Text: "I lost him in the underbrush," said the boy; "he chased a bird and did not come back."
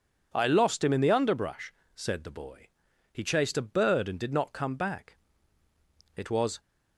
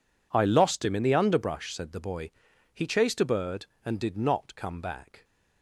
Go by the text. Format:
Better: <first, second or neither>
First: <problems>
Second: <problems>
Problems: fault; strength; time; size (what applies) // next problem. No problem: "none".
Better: second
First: goes on to say "It was"; slight; from 6.1 s on; 0.44 s long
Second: none